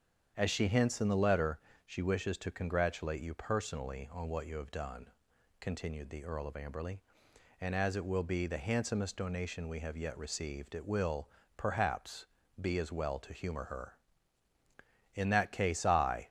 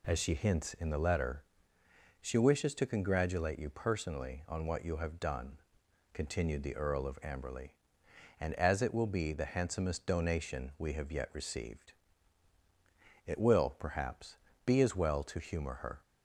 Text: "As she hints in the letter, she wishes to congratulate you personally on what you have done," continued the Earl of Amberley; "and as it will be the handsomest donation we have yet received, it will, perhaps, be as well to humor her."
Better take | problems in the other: second | starts louder than the rest; strong; until 1.3 s; 8 dB // goes on to say "In that case I"; noticeable; from 15.1 s on; 1.1 s long

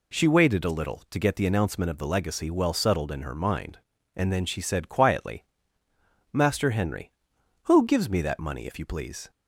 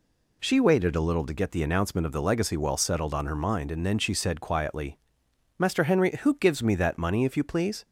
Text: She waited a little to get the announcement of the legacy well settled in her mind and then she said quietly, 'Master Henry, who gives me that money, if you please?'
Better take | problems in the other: first | says "on" for "in"; at 3.1 s

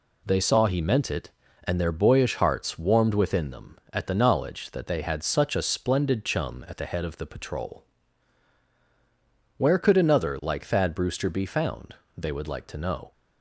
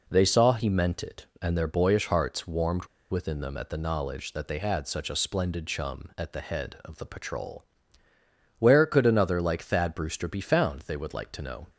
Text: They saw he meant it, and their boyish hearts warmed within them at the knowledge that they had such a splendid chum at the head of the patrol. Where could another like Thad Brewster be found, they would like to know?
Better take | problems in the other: first | pauses between "warmed" and "within"; slight; at 2.8 s; 0.24 s long

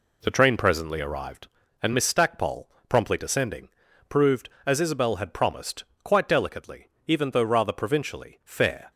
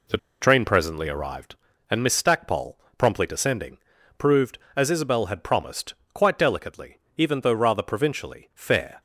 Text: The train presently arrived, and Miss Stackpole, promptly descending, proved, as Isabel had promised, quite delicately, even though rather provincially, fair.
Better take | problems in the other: first | pauses between "The" and "train"; slight; at 0.1 s; 0.23 s long

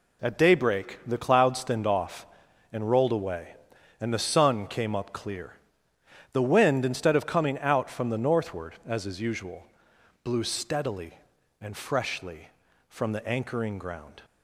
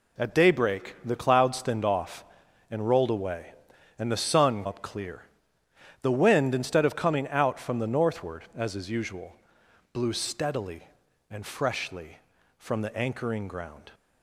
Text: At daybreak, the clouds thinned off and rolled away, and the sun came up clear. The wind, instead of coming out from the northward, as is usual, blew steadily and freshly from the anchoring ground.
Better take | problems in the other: first | skips "came"; at 4.6 s

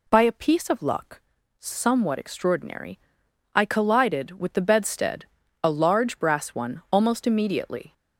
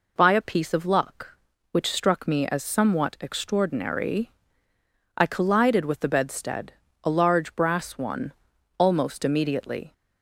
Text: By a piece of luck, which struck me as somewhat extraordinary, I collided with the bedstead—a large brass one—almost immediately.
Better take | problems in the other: second | skips "which struck me as"; at 1.3 s

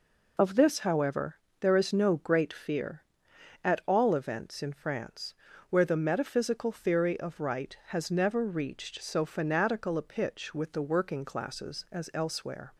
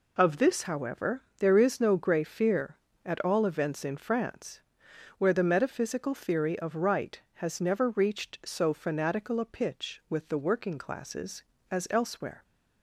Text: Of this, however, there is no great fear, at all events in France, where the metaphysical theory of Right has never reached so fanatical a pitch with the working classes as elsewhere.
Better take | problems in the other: first | says "grey" for "great"; at 1.9 s

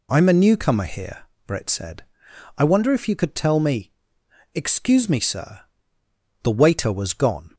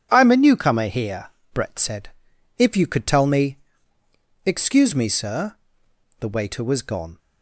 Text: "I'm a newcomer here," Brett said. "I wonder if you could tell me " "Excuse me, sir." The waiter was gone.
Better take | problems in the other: first | starts louder than the rest; strong; until 1.1 s; 8.5 dB // skips "I wonder"; at 2.3 s

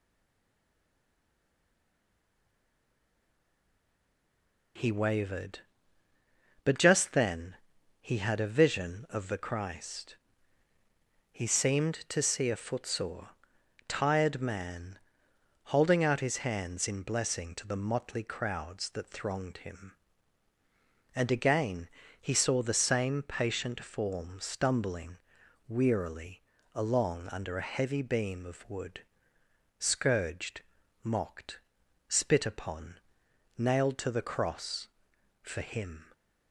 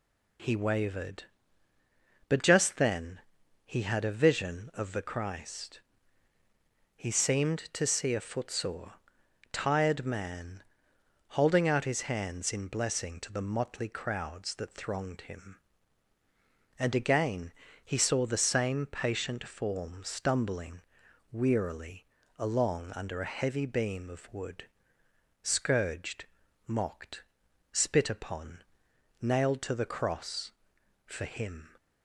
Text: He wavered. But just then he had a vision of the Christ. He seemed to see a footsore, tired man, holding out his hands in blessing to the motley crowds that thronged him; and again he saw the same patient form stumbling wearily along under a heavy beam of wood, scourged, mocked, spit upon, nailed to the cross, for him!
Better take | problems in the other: second | stays silent before the first word; strong; until 4.7 s; 4.7 s long // pauses between "then" and "he"; noticeable; at 7.5 s; 0.48 s long; noticeable in the second // pauses between "again" and "he"; slight; at 21.8 s; 0.32 s long; slight in the second // pauses between "stumbling" and "wearily"; noticeable; at 25.1 s; 0.54 s long; noticeable in the second // pauses between "wearily" and "along"; slight; at 26.4 s; 0.32 s long; slight in the second

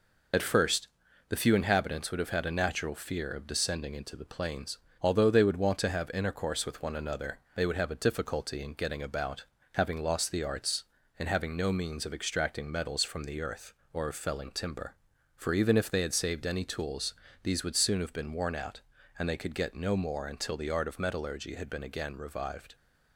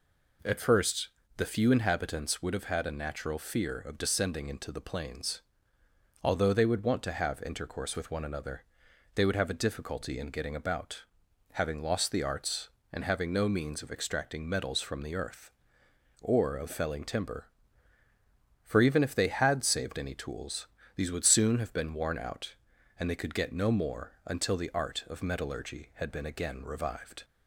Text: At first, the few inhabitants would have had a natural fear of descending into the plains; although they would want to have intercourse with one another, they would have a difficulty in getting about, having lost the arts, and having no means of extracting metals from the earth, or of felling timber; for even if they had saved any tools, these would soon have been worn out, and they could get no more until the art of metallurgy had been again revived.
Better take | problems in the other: second | loses the start of "At"; at 0.3 s; 35 ms

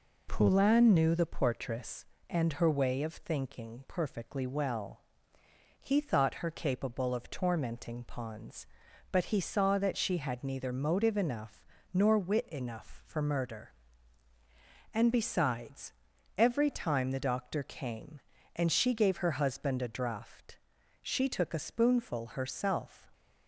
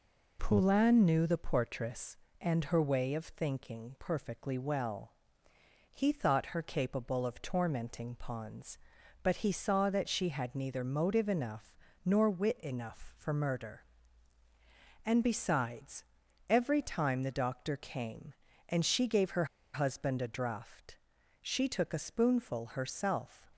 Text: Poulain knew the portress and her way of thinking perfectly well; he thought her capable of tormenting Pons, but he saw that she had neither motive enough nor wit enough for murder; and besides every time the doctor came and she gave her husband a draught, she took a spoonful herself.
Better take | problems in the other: first | pauses between "enough" and "nor"; slight; at 11.7 s; 0.28 s long; slight in the first // pauses between "besides" and "every"; noticeable; at 16.0 s; 0.46 s long; noticeable in the first // pauses between "her" and "husband"; slight; at 19.4 s; 0.29 s long

